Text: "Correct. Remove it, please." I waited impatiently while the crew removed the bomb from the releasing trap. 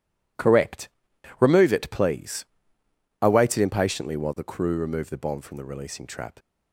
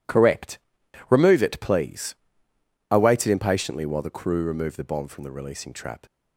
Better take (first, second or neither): neither